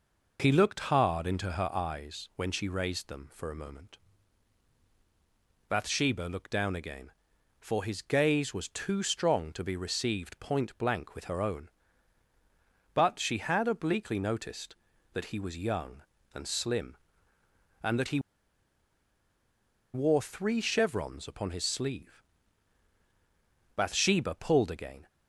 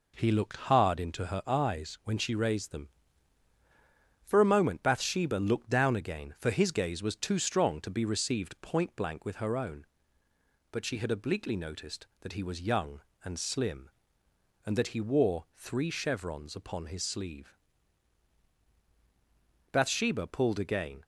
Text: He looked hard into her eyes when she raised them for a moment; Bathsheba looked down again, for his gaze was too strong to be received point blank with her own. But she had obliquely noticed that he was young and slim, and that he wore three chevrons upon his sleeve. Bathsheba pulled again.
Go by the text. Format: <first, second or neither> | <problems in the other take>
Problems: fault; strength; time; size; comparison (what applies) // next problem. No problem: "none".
second | pauses between "he" and "wore"; strong; at 18.1 s; 1.7 s long